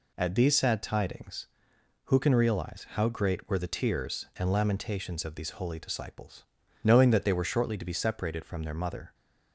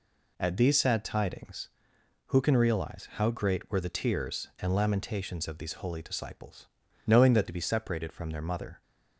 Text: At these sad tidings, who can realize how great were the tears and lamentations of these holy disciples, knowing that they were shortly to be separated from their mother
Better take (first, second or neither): first